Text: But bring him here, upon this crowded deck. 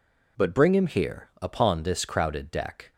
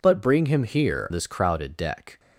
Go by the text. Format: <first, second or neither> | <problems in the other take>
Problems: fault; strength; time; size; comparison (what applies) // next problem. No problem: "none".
first | skips "upon"; at 1.1 s